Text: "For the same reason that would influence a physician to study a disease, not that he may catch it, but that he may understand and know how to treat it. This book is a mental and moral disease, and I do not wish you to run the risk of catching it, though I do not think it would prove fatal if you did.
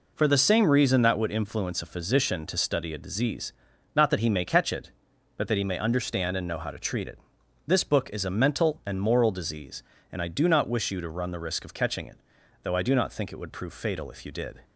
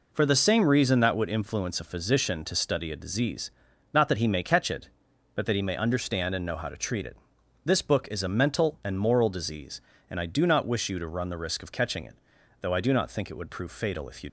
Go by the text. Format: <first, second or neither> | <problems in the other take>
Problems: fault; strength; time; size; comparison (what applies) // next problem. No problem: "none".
first | stops before "did"; at 14.2 s